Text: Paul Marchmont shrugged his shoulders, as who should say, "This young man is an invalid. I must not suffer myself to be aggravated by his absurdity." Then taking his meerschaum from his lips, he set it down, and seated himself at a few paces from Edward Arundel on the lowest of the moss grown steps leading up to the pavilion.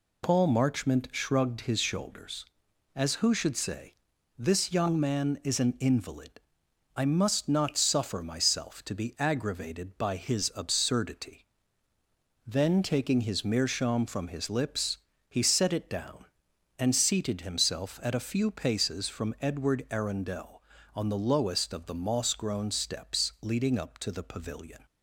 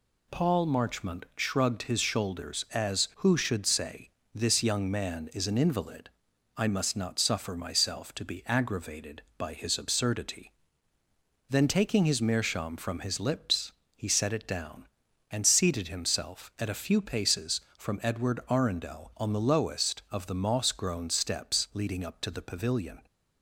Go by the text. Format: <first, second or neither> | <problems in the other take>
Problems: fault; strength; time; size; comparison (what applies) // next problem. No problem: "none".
neither | none